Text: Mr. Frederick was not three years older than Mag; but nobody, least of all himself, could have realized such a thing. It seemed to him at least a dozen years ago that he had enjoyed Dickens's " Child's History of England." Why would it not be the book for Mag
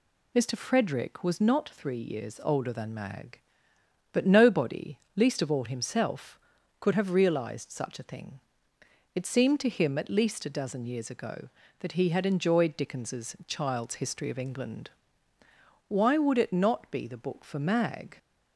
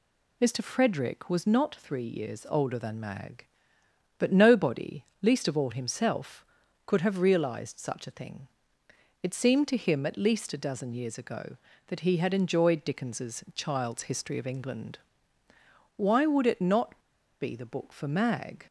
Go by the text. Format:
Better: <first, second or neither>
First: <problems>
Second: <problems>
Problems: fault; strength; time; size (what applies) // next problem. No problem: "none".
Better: first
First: none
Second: pauses between "not" and "be"; at 16.9 s; 0.42 s long